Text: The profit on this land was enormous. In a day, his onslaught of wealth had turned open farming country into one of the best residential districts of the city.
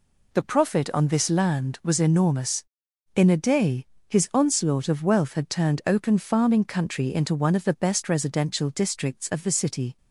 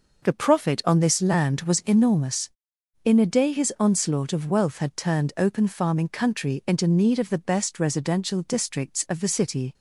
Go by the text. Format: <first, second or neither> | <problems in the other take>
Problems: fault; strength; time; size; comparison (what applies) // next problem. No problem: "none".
first | says "need" for "one"; at 6.8 s